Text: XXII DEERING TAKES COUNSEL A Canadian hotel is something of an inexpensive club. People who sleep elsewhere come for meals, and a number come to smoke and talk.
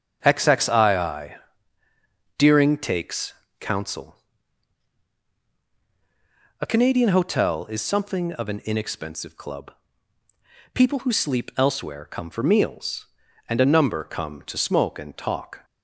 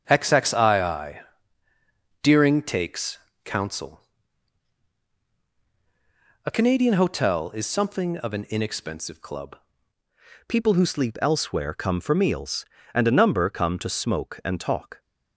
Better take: first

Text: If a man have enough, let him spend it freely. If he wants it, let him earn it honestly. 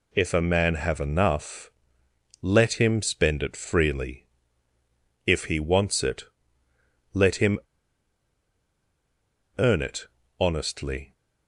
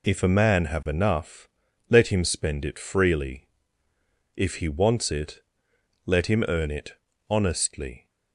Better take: second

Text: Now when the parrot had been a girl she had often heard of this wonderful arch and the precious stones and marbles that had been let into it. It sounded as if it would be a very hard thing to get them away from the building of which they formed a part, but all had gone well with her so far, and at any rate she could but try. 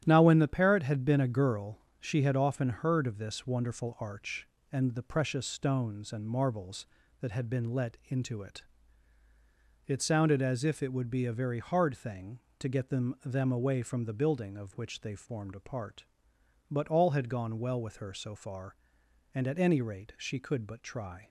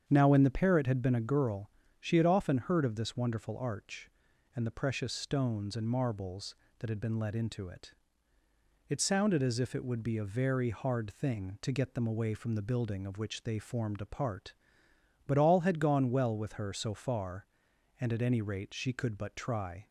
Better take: second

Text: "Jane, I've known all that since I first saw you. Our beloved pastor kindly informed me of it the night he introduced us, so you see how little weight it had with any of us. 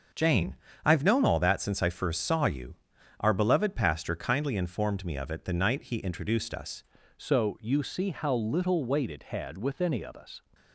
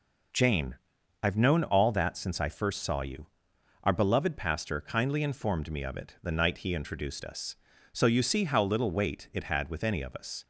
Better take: second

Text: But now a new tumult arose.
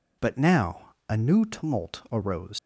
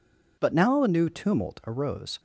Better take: second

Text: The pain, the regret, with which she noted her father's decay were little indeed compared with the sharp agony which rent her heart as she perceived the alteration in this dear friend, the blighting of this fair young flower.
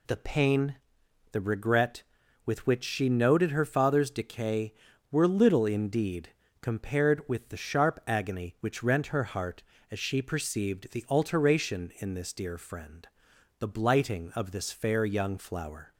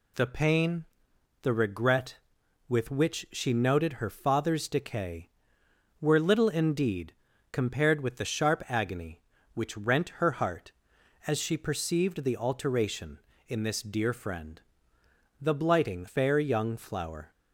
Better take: first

